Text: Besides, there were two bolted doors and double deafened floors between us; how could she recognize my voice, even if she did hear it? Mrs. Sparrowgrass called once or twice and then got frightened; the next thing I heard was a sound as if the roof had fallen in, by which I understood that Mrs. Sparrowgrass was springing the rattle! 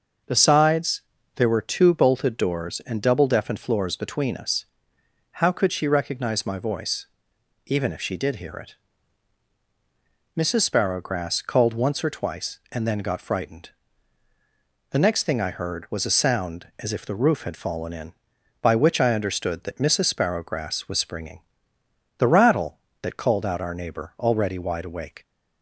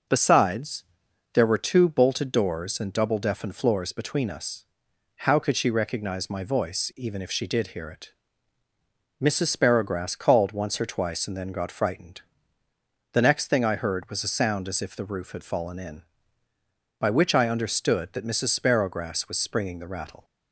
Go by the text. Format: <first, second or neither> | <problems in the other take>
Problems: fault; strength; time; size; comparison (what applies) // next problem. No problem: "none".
second | starts louder than the rest; until 1.6 s; 6 dB // pauses between "springing" and "the"; noticeable; at 21.4 s; 0.78 s long // goes on to say "That called out our neighbor already wide awake"; strong; from 23.0 s on; 2.2 s long